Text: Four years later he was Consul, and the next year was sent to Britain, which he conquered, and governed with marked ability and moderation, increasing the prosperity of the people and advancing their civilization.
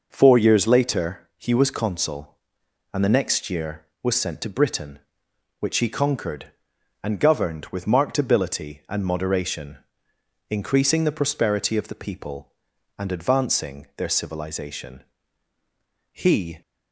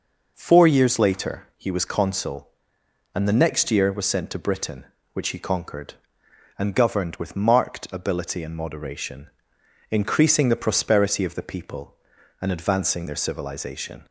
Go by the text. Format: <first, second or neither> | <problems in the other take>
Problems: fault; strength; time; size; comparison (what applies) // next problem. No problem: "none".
second | goes on to say "He"; from 16.1 s on; 0.50 s long